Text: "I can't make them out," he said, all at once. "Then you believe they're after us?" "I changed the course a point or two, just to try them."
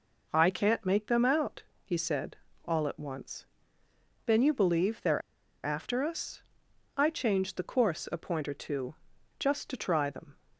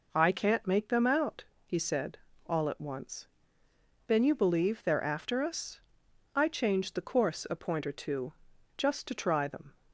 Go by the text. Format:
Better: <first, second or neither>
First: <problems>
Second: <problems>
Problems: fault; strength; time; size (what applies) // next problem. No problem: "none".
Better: second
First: pauses between "they're" and "after"; at 5.2 s; 0.43 s long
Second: none